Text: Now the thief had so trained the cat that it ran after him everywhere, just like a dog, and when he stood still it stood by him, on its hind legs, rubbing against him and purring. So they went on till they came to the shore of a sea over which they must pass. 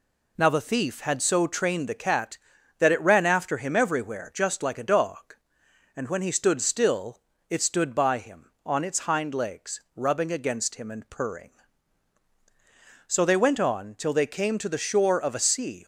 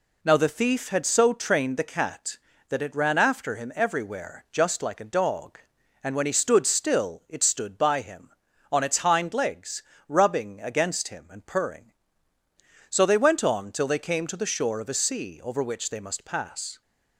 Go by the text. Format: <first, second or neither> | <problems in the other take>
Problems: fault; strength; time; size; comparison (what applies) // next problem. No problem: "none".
second | pauses between "still" and "it"; slight; at 7.1 s; 0.30 s long // stops before "over which they must pass"; at 15.8 s